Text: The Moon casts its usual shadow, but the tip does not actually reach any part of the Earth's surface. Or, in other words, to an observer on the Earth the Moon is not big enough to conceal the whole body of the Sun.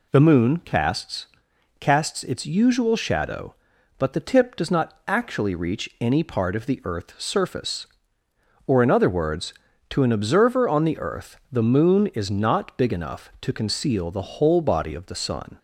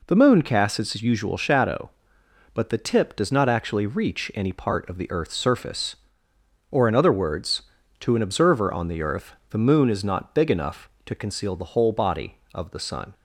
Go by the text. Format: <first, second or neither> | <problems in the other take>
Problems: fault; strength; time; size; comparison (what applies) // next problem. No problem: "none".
second | says "casts" twice; at 1.8 s // pauses between "Earth" and "the"; slight; at 11.3 s; 0.16 s long; slight in the second